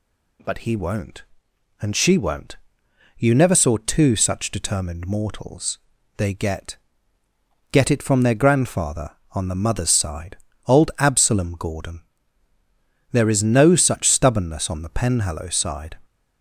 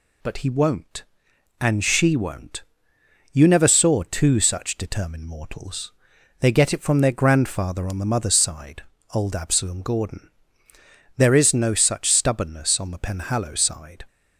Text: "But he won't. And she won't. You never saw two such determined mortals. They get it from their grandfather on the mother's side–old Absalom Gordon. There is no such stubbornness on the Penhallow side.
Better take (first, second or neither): second